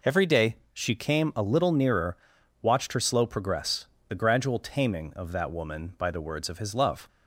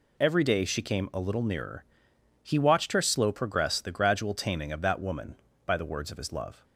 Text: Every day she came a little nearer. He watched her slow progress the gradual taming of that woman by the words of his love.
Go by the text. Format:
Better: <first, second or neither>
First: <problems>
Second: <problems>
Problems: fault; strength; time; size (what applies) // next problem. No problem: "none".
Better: second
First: pauses between "day" and "she"; slight; at 0.5 s; 0.18 s long // skips "He"; at 2.3 s // pauses between "progress" and "the"; slight; at 3.8 s; 0.22 s long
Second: none